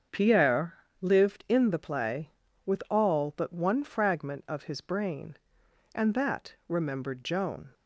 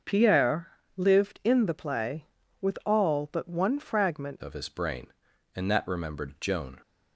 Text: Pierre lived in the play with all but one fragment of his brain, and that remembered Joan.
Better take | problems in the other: first | starts louder than the rest; until 1.3 s; 6.5 dB; strong in the first // pauses between "Pierre" and "lived"; slight; at 0.6 s; 0.30 s long; slight in the first // changes voice at "of"; from 4.4 s on; 2.4 s long

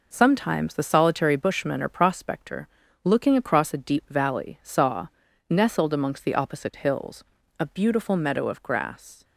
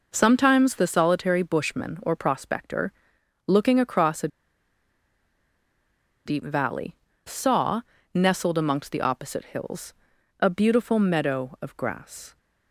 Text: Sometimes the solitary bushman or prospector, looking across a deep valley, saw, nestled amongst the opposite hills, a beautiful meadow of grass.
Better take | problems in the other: first | pauses between "a" and "deep"; strong; at 4.2 s; 1.9 s long

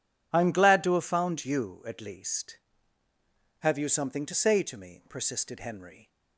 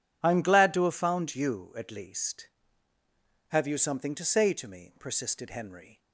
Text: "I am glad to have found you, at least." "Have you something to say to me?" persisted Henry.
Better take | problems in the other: neither | none

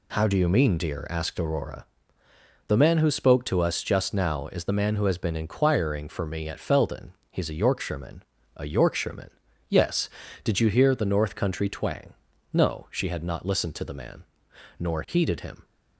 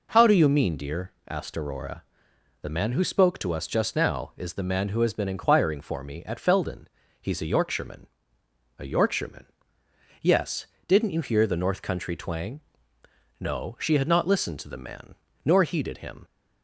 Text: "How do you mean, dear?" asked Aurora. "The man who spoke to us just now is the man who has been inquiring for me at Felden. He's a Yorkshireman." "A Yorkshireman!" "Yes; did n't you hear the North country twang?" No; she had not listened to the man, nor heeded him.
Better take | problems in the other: second | skips "n't"; at 10.5 s

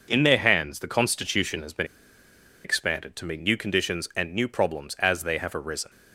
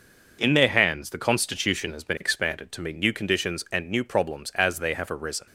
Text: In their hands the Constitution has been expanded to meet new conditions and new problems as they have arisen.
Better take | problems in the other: second | pauses between "been" and "expanded"; noticeable; at 1.8 s; 0.79 s long

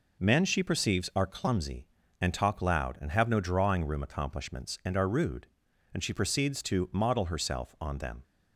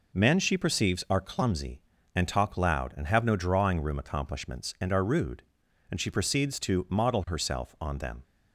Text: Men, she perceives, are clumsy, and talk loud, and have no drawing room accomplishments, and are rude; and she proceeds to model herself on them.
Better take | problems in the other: neither | none

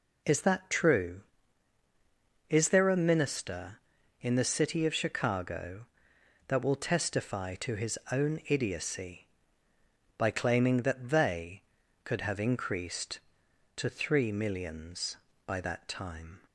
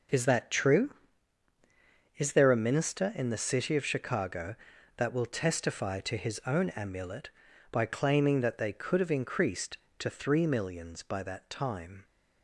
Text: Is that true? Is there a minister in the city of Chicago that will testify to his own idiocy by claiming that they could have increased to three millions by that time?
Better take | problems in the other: first | says "amulet" for "idiocy"; at 6.6 s

